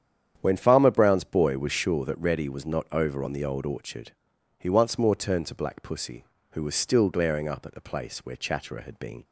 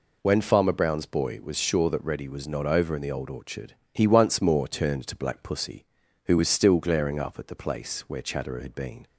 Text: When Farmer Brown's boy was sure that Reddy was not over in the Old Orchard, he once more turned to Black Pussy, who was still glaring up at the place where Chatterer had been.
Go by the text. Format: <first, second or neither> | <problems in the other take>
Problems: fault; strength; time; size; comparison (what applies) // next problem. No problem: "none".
second | starts louder than the rest; strong; until 1.4 s; 9 dB // says "on" for "in"; at 3.2 s